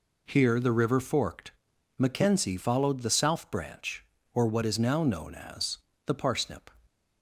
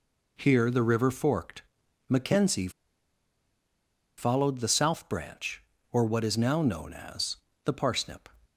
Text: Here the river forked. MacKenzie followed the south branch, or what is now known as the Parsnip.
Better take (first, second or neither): first